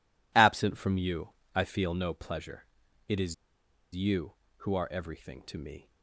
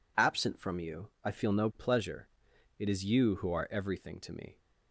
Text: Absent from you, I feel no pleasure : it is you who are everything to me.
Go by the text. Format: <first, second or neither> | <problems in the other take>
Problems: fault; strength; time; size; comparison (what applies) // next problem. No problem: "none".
second | pauses between "is" and "you"; noticeable; at 3.3 s; 0.59 s long